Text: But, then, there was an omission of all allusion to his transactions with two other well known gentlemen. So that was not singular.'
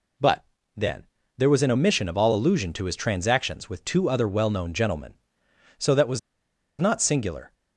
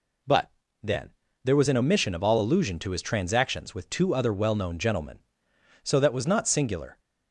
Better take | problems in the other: second | pauses between "was" and "not"; noticeable; at 6.1 s; 0.61 s long

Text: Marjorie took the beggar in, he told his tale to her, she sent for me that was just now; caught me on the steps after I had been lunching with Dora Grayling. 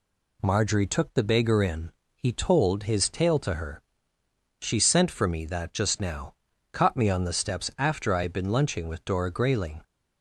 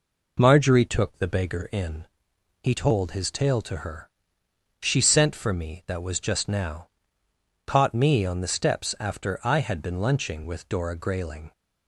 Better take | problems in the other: second | skips "was"; at 5.7 s

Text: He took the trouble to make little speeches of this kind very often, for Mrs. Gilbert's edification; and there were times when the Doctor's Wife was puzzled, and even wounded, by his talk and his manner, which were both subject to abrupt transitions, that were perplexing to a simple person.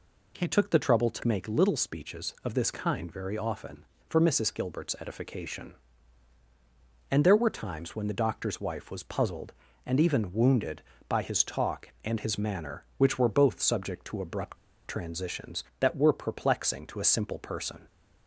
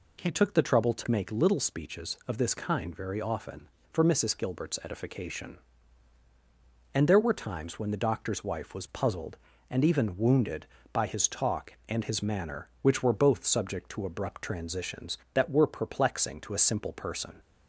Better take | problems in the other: second | pauses between "abrupt" and "transitions"; slight; at 14.5 s; 0.31 s long

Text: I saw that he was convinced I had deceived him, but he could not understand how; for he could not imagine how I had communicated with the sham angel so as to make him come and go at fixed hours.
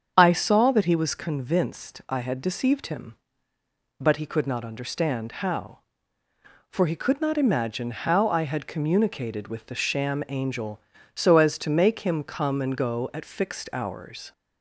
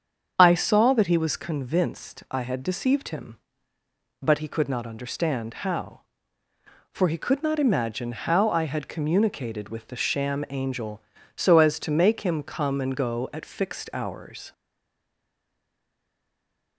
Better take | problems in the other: first | starts louder than the rest; strong; until 1.4 s; 7.5 dB; strong in the first // stays silent after the last word; from 14.5 s on; 2.2 s long

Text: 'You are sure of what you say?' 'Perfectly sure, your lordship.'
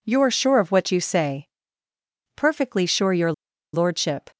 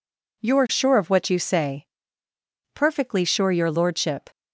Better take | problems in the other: second | pauses between "your" and "lordship"; at 3.3 s; 0.41 s long

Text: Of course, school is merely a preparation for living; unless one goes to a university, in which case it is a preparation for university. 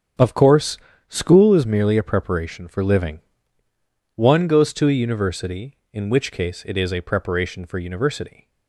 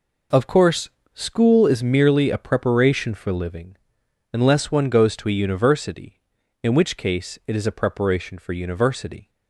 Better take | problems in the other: second | starts louder than the rest; strong; until 1.5 s; 8 dB // skips "unless"; at 3.6 s

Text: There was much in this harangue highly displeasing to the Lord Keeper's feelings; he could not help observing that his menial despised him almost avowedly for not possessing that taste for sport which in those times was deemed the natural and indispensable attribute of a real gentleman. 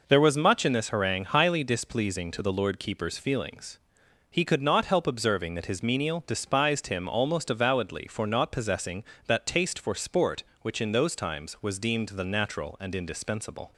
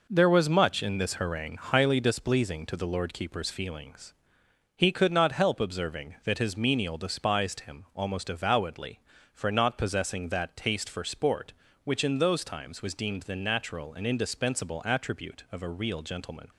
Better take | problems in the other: second | stops before "attribute of a real gentleman"; at 13.7 s

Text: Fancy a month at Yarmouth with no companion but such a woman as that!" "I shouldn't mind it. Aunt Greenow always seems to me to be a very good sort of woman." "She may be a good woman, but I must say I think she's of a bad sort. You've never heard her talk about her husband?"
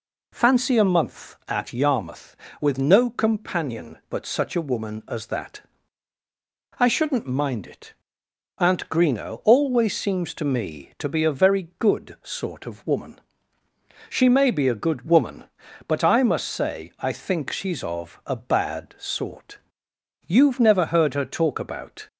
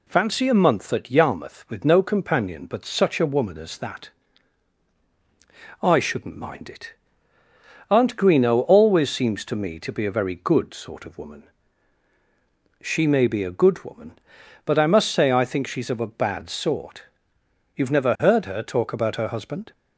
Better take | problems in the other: second | stops before "her husband"; at 22.0 s

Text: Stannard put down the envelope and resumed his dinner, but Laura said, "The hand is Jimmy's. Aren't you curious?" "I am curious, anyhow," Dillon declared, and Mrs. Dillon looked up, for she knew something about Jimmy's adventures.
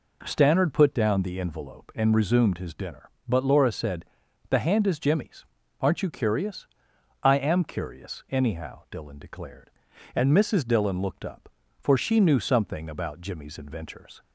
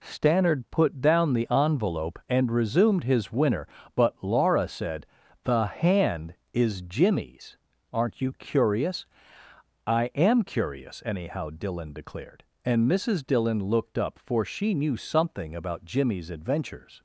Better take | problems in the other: first | says "winner" for "dinner"; at 3.3 s

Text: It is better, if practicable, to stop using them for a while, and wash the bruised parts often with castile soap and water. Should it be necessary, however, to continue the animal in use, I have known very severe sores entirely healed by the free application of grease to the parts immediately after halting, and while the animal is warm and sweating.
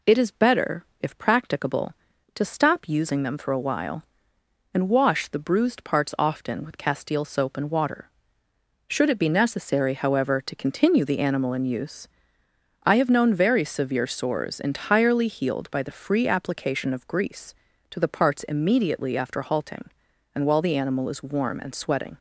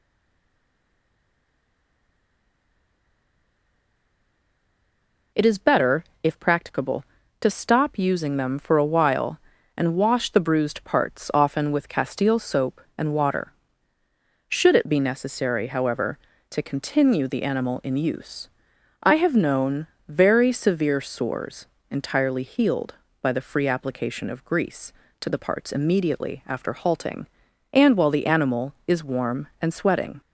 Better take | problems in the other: first | stays silent before the first word; strong; until 5.3 s; 5.3 s long // pauses between "known" and "very"; slight; at 19.8 s; 0.22 s long // pauses between "sores" and "entirely"; slight; at 21.6 s; 0.22 s long

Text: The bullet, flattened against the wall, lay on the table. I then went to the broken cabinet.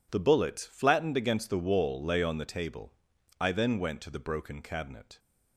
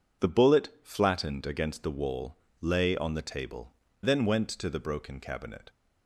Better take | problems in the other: first | skips "I"; at 3.8 s

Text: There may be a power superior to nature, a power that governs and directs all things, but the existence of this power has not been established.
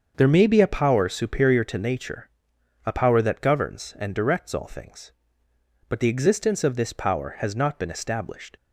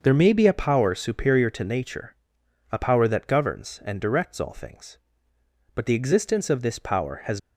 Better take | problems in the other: first | starts louder than the rest; noticeable; until 1.0 s; 6 dB; also in the first // stops before "not been established"; at 7.3 s

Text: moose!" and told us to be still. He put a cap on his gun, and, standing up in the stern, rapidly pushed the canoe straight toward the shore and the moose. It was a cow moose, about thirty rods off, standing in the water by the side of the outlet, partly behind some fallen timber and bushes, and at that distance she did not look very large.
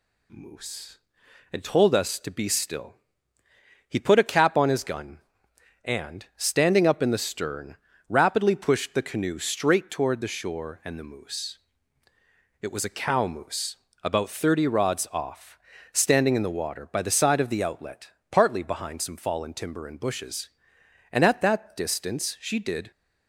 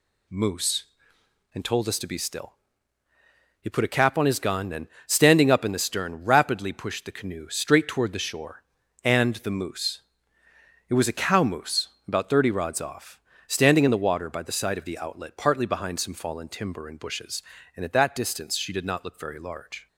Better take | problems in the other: second | stops before "not look very large"; at 22.9 s

